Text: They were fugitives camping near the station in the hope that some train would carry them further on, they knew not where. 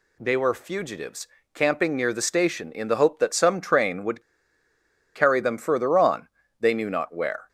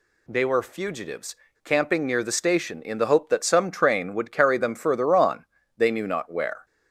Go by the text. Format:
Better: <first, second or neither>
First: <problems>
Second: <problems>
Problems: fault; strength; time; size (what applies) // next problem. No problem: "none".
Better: second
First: pauses between "fugitives" and "camping"; slight; at 1.2 s; 0.26 s long // pauses between "would" and "carry"; noticeable; at 4.2 s; 0.94 s long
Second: pauses between "fugitives" and "camping"; slight; at 1.3 s; 0.27 s long